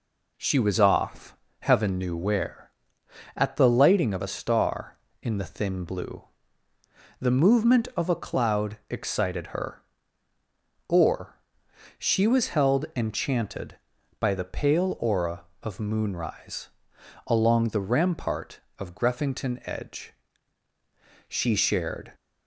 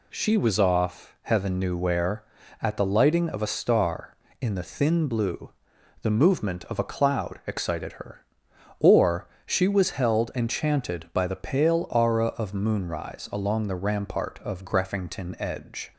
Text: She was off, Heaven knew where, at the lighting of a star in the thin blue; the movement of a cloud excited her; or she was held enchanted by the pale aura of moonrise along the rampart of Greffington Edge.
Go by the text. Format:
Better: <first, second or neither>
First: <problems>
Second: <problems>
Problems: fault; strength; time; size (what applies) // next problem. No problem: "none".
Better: second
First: pauses between "or" and "she"; noticeable; at 11.3 s; 0.60 s long // pauses between "moonrise" and "along"; noticeable; at 16.6 s; 0.58 s long // goes on to say "She shared"; noticeable; from 21.2 s on; 0.86 s long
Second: pauses between "or" and "she"; slight; at 9.2 s; 0.18 s long